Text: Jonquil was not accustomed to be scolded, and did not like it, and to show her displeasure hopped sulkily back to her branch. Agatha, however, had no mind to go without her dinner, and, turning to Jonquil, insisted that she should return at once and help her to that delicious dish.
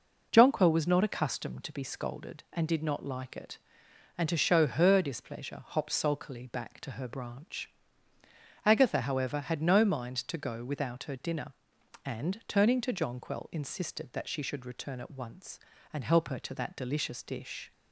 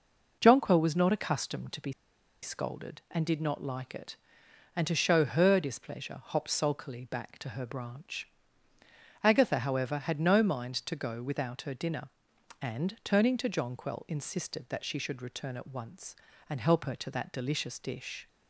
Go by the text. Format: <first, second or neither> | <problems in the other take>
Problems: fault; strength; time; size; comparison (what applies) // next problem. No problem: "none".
first | pauses between "be" and "scolded"; noticeable; at 1.9 s; 0.50 s long